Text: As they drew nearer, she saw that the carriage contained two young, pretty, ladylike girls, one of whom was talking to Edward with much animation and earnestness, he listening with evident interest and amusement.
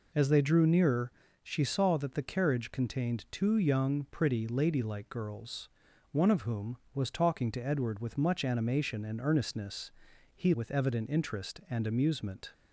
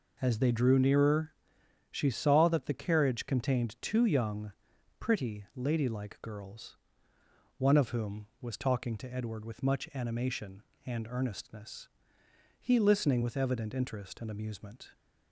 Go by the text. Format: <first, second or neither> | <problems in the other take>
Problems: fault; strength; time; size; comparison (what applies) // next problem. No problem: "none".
second | skips "listening"; at 10.5 s